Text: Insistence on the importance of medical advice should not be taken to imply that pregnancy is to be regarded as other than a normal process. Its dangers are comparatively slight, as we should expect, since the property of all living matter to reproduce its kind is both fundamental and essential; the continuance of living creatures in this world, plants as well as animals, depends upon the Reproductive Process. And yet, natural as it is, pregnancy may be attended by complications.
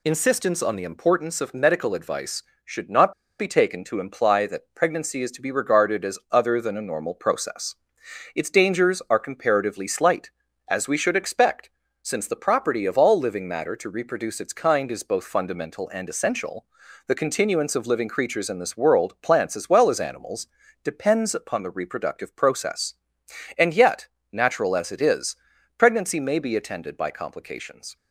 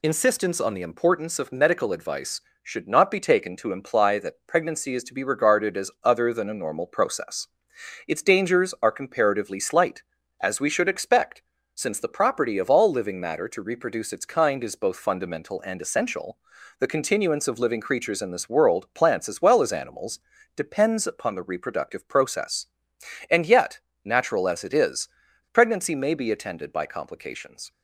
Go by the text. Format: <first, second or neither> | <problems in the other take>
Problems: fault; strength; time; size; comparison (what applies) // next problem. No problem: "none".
second | pauses between "not" and "be"; slight; at 3.1 s; 0.27 s long